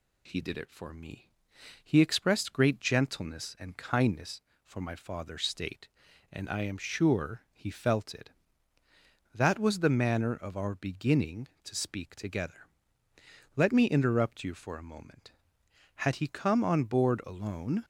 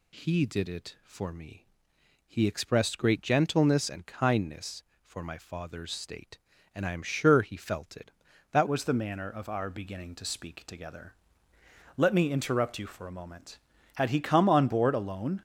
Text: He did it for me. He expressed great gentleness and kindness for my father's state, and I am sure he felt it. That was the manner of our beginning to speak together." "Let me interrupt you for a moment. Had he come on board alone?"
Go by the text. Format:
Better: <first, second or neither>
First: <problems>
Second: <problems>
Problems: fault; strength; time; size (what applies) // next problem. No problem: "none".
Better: first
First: none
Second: changes voice at "was"; from 8.6 s on; 6.8 s long